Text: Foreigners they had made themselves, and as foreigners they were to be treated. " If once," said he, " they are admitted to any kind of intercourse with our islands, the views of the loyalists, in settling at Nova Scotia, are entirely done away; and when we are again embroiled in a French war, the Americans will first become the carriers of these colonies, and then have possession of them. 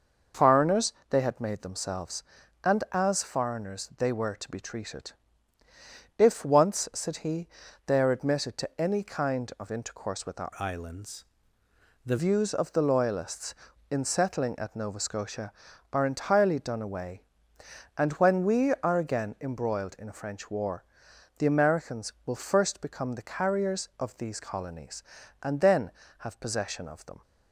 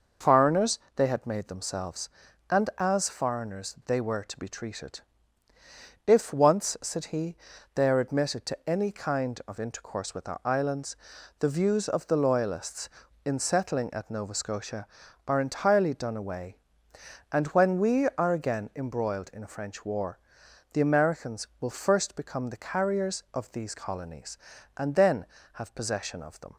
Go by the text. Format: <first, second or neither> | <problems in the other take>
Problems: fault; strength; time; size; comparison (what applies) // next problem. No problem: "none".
second | pauses between "Foreigners" and "they"; slight; at 0.9 s; 0.20 s long; slight in the second // changes voice from "islands" to "the"; from 10.5 to 12.1 s; 1.6 s long